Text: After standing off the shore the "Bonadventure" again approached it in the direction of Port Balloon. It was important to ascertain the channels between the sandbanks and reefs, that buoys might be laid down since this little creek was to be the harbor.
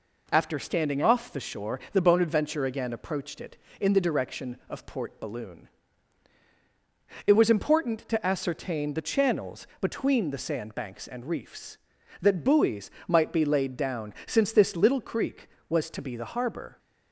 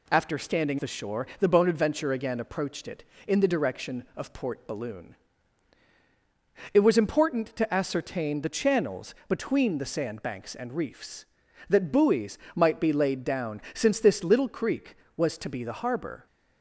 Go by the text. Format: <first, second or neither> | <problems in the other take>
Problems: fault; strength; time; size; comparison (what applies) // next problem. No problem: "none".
first | skips "off"; at 0.7 s // pauses between "buoys" and "might"; slight; at 12.3 s; 0.16 s long; slight in the first